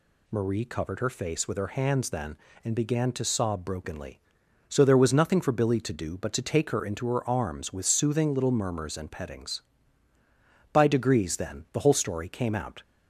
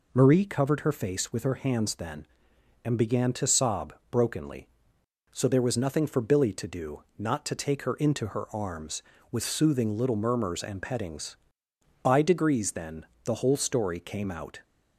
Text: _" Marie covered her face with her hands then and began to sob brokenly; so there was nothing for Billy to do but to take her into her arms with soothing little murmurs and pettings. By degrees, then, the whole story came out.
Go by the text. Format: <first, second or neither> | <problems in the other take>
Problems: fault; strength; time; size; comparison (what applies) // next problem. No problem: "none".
first | pauses between "sob" and "brokenly"; slight; at 3.9 s; 0.18 s long // says "not" for "but"; at 7.1 s